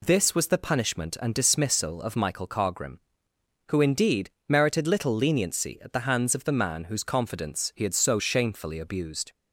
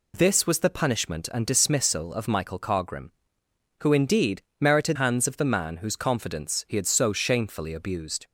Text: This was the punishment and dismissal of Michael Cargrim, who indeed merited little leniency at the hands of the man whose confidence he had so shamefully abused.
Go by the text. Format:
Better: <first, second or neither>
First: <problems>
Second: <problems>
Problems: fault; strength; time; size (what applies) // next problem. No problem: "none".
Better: first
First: pauses between "indeed" and "merited"; slight; at 4.2 s; 0.20 s long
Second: pauses between "indeed" and "merited"; slight; at 4.4 s; 0.20 s long // skips "little leniency at the"; at 4.9 s